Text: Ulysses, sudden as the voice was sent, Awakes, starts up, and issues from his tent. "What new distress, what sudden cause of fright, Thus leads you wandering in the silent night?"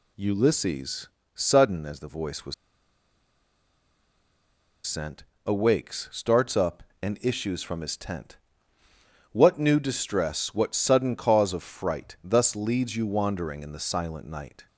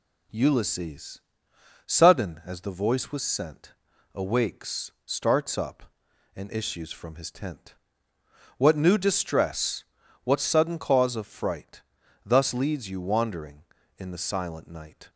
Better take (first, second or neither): second